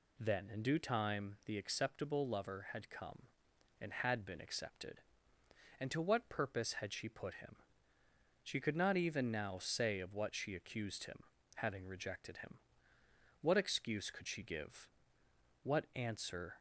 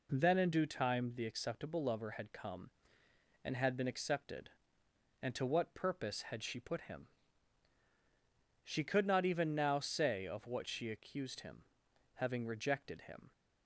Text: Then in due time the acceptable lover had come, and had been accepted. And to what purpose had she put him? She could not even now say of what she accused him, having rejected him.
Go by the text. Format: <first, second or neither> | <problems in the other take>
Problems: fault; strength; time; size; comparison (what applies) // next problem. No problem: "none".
second | goes on to say "What excuse could she give What answer"; strong; from 13.4 s on; 3.1 s long